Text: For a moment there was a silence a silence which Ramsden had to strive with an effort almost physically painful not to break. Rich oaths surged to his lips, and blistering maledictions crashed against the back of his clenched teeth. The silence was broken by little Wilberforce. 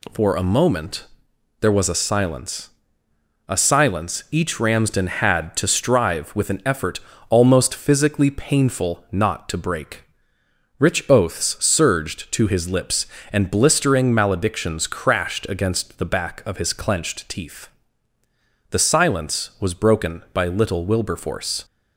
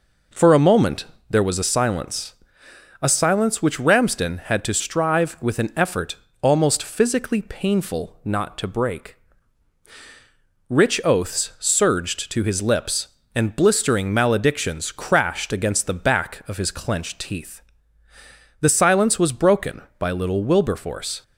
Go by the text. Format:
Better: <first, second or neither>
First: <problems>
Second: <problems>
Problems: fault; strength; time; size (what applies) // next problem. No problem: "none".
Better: second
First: pauses between "moment" and "there"; noticeable; at 1.0 s; 0.54 s long // pauses between "silence" and "a"; noticeable; at 2.6 s; 0.80 s long // says "each" for "which"; at 4.3 s // pauses between "effort" and "almost"; slight; at 7.0 s; 0.28 s long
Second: pauses between "moment" and "there"; slight; at 1.0 s; 0.26 s long // pauses between "silence" and "a"; noticeable; at 2.3 s; 0.70 s long // pauses between "effort" and "almost"; slight; at 6.1 s; 0.26 s long